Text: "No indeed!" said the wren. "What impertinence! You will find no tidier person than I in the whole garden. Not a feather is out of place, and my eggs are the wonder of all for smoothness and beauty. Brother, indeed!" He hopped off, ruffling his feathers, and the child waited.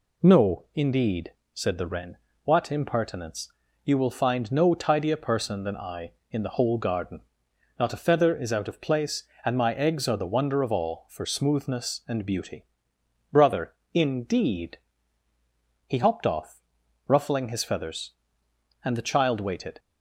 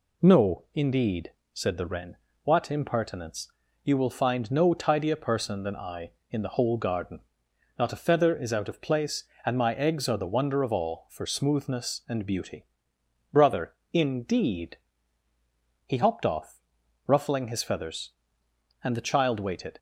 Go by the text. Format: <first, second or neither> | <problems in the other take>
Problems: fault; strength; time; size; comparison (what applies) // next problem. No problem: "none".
neither | none